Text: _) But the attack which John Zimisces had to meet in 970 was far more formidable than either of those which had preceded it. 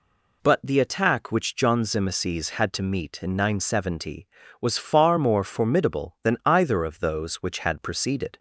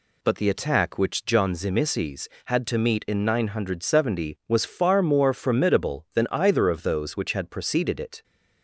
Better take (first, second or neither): second